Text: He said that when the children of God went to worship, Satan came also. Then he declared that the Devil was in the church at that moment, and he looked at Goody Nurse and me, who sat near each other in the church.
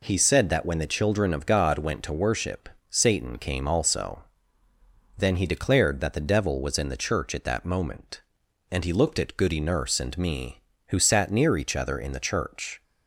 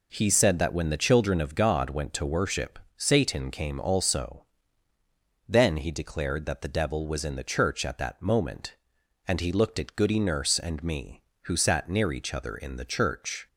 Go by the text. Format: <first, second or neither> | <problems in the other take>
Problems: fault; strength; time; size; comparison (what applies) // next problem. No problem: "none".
neither | none